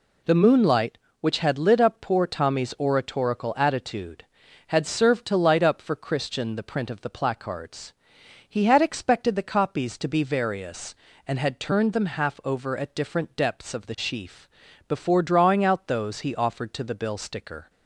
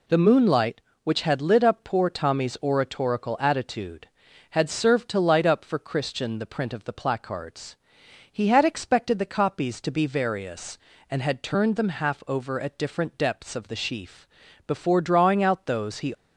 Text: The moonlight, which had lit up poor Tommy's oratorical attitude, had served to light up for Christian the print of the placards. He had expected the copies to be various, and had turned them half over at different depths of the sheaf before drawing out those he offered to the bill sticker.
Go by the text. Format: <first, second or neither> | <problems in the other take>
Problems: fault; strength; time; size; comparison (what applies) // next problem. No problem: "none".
first | pauses between "sheaf" and "before"; at 14.2 s; 0.40 s long; also in the first // stops before "offered to the bill sticker"; at 16.1 s